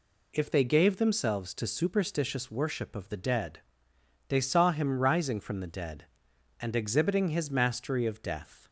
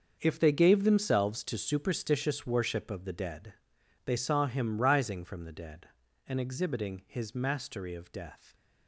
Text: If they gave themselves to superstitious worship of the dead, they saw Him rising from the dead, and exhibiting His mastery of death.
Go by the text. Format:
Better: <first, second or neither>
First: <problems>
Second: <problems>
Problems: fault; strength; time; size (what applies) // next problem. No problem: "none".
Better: first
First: none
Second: gets quieter; strong; throughout; 12.5 dB